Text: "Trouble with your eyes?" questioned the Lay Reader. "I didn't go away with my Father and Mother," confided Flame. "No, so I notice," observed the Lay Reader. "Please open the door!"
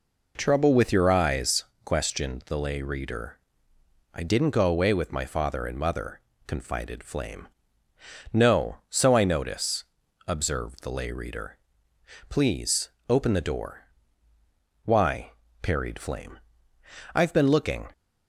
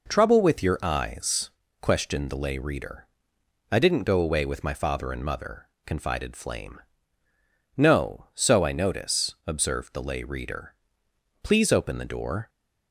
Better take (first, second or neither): second